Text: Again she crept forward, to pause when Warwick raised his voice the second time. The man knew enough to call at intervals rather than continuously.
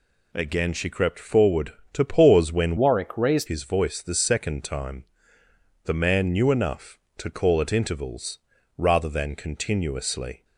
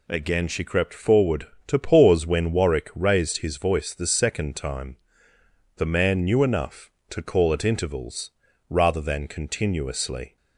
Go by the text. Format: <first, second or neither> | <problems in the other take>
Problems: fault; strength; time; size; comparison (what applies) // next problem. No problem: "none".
second | changes voice from "Warwick" to "raised"; from 2.7 to 3.4 s; 0.7 s long // pauses between "intervals" and "rather"; at 8.3 s; 0.38 s long; also in the second